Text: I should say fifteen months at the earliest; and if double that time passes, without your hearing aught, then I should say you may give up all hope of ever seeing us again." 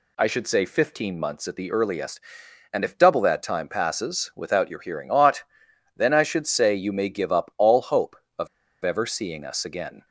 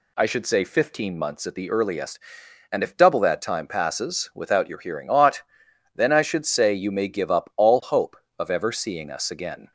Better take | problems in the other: second | pauses between "of" and "ever"; slight; at 8.4 s; 0.35 s long

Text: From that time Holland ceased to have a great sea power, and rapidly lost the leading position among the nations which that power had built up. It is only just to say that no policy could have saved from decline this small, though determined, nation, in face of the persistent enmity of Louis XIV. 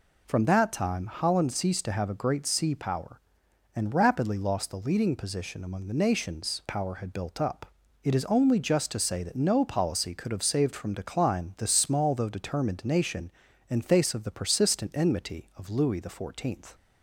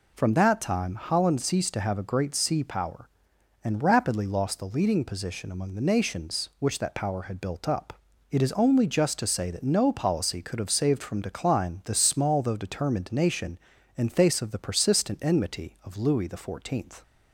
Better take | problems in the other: second | skips "which that"; at 6.6 s

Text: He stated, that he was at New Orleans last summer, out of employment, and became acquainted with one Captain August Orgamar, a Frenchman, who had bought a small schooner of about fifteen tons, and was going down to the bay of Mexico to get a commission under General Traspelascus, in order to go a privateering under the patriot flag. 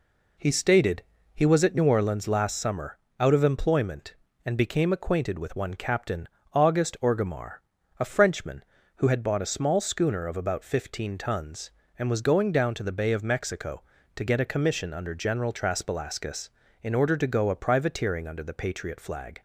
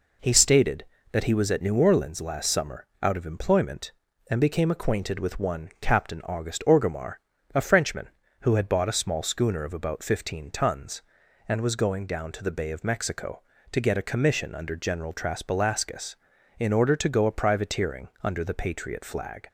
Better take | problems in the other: second | skips "that"; at 1.1 s // pauses between "Captain" and "August"; slight; at 6.2 s; 0.26 s long

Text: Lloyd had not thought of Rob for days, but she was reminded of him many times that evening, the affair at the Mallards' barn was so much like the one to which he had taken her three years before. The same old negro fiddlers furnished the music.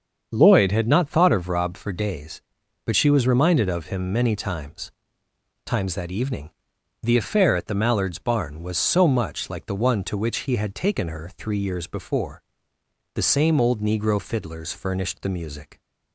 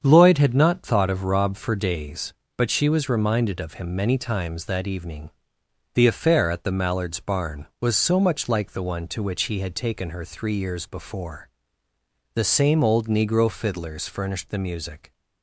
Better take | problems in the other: second | starts louder than the rest; until 1.3 s; 7 dB; strong in the second // says "times" twice; at 5.6 s

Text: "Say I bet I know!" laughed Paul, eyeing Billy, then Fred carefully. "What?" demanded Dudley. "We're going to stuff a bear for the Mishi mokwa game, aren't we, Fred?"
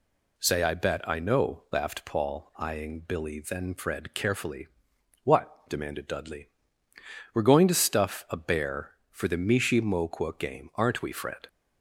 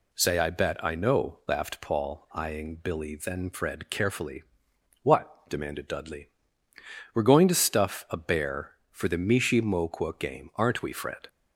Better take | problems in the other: neither | none

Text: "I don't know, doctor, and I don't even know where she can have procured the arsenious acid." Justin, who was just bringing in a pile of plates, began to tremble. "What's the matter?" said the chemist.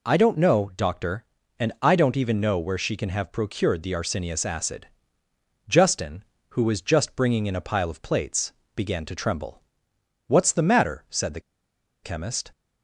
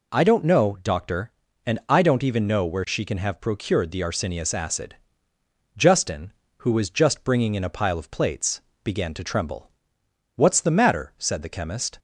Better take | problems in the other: second | pauses between "the" and "chemist"; noticeable; at 11.3 s; 0.63 s long

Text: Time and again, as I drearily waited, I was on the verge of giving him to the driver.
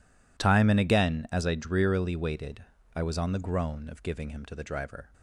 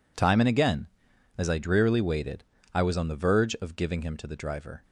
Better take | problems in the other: second | says "groan" for "verge"; at 3.3 s

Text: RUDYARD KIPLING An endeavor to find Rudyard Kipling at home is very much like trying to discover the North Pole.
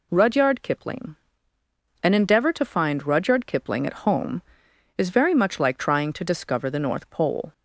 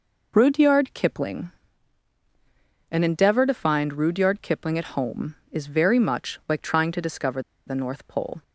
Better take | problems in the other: first | pauses between "KIPLING" and "An"; strong; at 1.5 s; 1.3 s long; noticeable in the first // pauses between "discover" and "the"; slight; at 7.4 s; 0.26 s long

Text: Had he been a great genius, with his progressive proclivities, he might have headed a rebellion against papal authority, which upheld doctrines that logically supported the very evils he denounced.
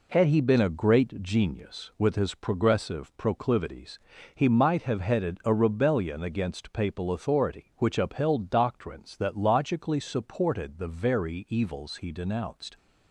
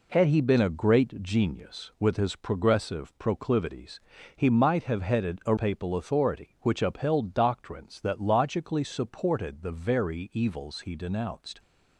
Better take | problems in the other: first | skips "rebellion against"; at 5.5 s

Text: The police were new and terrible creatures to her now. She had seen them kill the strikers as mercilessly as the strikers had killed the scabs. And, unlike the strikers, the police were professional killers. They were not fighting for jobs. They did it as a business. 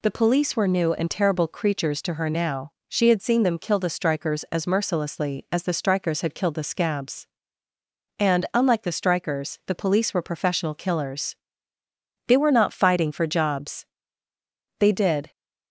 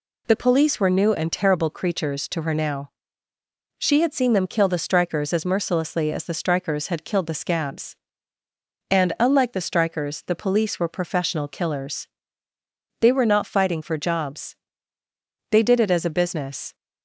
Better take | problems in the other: second | stops before "it as a business"; at 15.3 s

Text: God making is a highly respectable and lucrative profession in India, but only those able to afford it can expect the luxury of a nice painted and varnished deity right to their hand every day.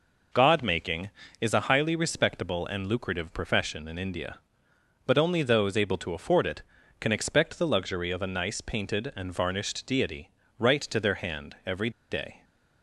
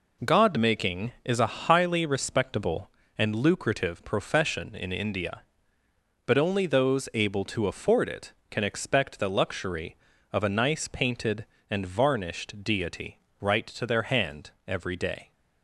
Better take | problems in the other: second | pauses between "deity" and "right"; slight; at 10.2 s; 0.30 s long; slight in the second // pauses between "every" and "day"; slight; at 11.8 s; 0.21 s long

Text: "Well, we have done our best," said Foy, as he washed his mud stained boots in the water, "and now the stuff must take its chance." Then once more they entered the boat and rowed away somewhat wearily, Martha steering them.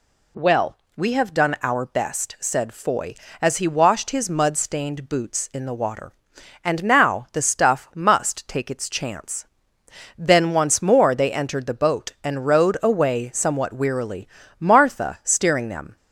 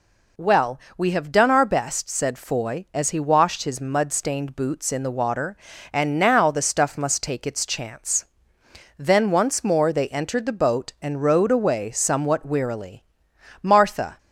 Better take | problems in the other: first | stops before "steering them"; at 14.1 s

